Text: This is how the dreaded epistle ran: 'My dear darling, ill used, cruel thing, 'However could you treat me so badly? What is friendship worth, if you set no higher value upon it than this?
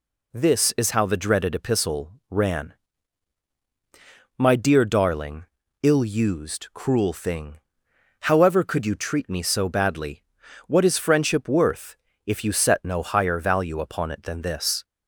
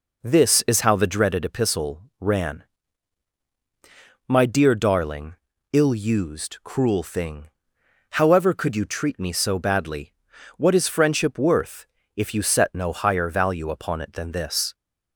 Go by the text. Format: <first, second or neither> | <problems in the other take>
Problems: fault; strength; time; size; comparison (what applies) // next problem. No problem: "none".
first | starts louder than the rest; noticeable; until 1.2 s; 4.5 dB // pauses between "epistle" and "ran"; slight; at 2.0 s; 0.18 s long; slight in the first